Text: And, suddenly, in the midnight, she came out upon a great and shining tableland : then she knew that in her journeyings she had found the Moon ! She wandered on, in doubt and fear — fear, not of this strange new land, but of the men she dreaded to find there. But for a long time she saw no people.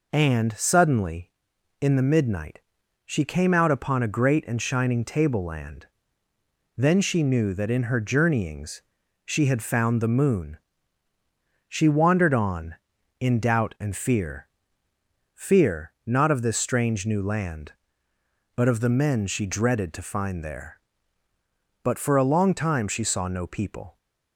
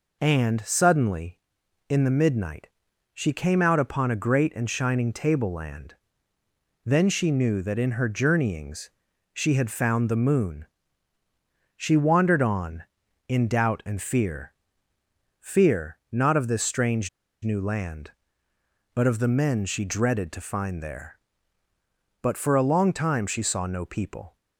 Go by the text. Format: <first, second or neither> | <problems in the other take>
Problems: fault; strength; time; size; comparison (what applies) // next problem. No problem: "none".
first | pauses between "journeyings" and "she"; noticeable; at 8.8 s; 0.46 s long; noticeable in the first // pauses between "strange" and "new"; slight; at 17.0 s; 0.34 s long